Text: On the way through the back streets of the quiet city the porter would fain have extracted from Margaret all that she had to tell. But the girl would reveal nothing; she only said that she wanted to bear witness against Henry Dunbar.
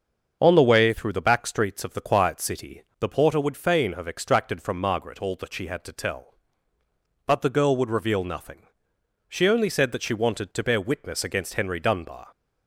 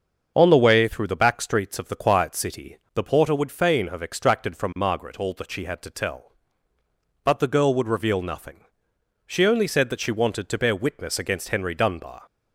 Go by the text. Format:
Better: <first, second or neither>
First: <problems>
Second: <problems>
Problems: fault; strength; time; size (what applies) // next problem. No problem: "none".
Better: neither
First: starts louder than the rest; until 1.4 s; 6.5 dB // pauses between "city" and "the"; slight; at 2.8 s; 0.16 s long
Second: starts louder than the rest; until 1.3 s; 6.5 dB // pauses between "city" and "the"; slight; at 2.7 s; 0.16 s long